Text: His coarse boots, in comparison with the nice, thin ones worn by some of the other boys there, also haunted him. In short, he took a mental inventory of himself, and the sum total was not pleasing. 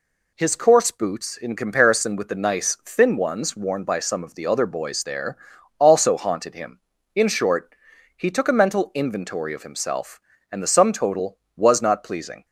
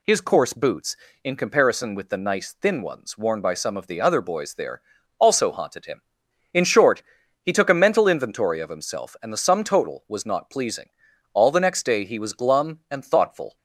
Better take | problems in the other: first | goes on to say "All the next day he was glum and thoughtful"; strong; from 11.3 s on; 2.2 s long

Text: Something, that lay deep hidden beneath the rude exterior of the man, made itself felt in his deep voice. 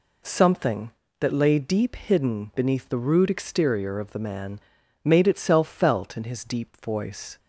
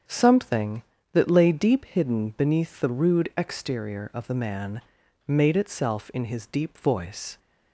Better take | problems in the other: first | starts louder than the rest; strong; until 1.3 s; 7 dB // skips "felt"; at 6.1 s

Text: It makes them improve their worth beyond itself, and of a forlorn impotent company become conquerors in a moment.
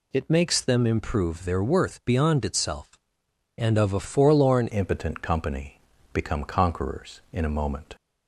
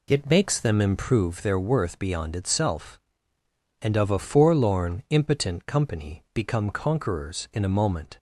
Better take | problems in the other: second | changes voice at "impotent"; from 4.7 s on; 3.2 s long // pauses between "company" and "become"; at 5.7 s; 0.38 s long

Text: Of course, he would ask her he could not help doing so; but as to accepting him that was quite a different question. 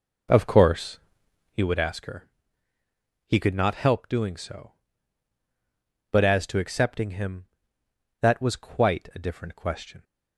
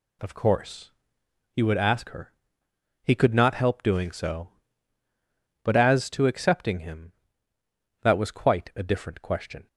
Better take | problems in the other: second | starts louder than the rest; noticeable; until 1.6 s; 4.5 dB // pauses between "her" and "he"; noticeable; at 2.2 s; 0.96 s long; noticeable in the second

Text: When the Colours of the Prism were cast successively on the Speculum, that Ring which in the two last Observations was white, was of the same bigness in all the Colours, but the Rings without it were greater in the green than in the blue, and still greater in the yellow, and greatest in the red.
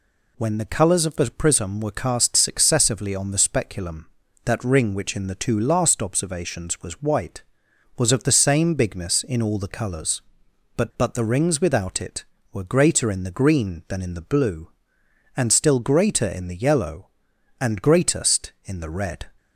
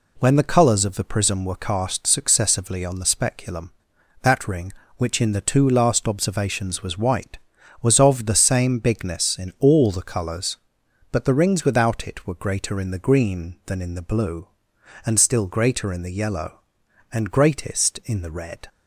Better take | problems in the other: second | says "but" twice; at 10.9 s

